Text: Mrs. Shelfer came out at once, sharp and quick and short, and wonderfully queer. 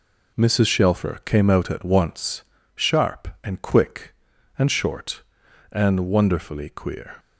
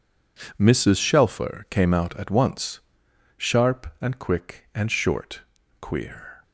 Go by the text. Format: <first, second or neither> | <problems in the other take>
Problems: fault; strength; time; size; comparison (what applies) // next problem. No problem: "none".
first | skips "and wonderfully"; at 5.6 s